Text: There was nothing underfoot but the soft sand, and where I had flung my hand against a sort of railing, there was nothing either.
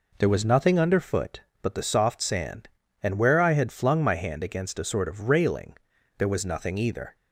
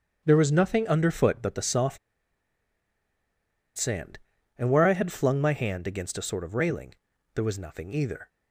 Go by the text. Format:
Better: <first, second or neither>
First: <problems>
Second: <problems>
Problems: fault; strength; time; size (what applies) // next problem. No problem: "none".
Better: first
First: none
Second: starts louder than the rest; strong; until 1.2 s; 7.5 dB // pauses between "soft" and "sand"; strong; at 1.9 s; 1.8 s long